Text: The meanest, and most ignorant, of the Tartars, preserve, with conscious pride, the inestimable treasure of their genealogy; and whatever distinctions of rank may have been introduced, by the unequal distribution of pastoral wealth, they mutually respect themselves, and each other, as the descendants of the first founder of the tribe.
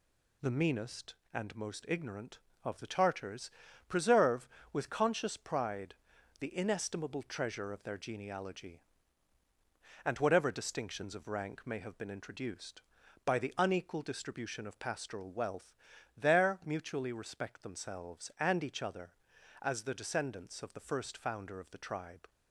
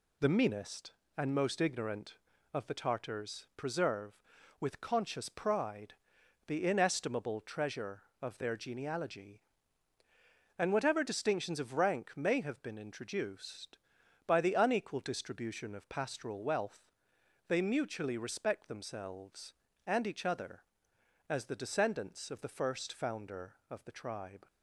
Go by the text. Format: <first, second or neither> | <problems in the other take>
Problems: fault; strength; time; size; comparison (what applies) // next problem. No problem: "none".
second | says "there" for "they"; at 16.1 s